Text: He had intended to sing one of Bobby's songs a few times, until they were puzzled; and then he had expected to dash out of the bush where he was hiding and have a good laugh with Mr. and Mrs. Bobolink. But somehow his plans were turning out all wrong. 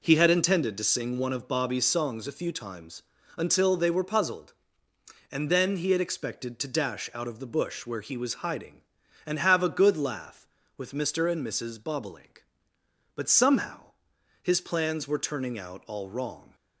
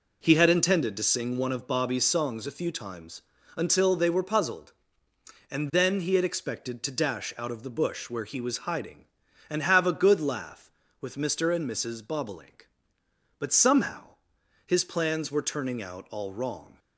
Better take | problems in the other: neither | pauses between "somehow" and "his"; noticeable; the same in both

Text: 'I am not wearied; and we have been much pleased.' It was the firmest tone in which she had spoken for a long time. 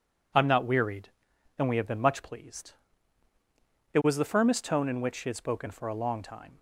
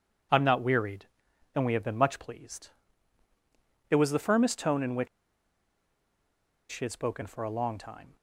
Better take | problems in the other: first | pauses between "which" and "she"; strong; at 5.0 s; 1.6 s long

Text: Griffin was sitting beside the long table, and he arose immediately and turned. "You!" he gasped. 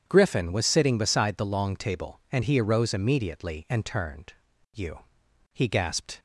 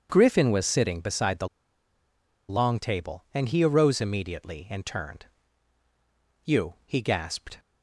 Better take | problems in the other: first | starts louder than the rest; strong; until 1.1 s; 7 dB; strong in the first // pauses between "the" and "long"; at 1.4 s; 1.0 s long

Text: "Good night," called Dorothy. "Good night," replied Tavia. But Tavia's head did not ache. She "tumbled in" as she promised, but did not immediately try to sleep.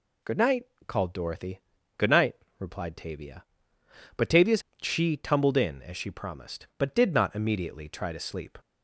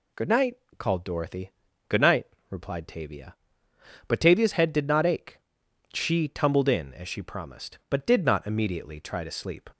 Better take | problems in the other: second | skips "head did not ache"; at 4.7 s

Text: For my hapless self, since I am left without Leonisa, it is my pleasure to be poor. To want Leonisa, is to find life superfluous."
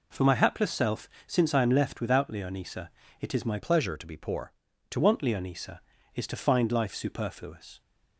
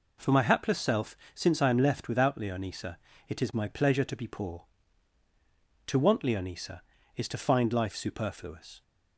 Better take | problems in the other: second | changes voice from "pleasure" to "To"; from 3.5 to 4.9 s; 1.4 s long

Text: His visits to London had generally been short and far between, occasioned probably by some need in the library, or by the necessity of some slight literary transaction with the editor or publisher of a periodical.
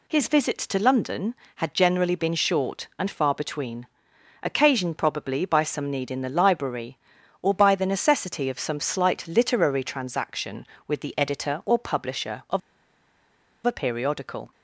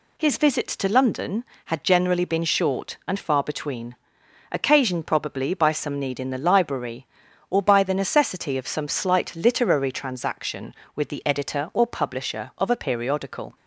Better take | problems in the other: second | pauses between "of" and "a"; at 12.6 s; 1.0 s long

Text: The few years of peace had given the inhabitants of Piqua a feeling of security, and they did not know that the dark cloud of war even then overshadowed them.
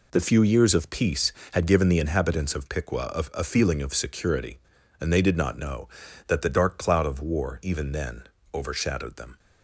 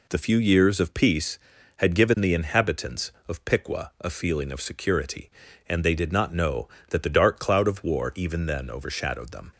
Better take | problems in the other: second | says "a" twice; at 3.4 s // pauses between "then" and "overshadowed"; slight; at 8.2 s; 0.28 s long

